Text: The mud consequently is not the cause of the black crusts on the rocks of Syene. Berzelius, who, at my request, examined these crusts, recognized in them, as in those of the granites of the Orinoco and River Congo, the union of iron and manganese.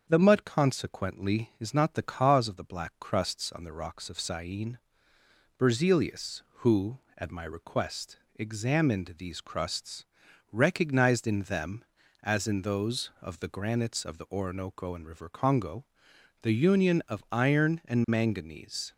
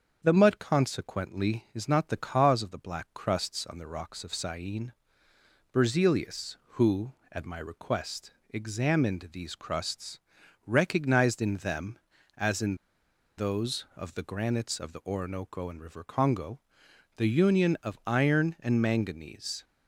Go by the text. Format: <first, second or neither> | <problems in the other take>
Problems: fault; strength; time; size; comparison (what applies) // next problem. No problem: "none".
first | starts louder than the rest; strong; until 1.2 s; 7 dB; strong in the first // pauses between "in" and "those"; noticeable; at 12.7 s; 0.60 s long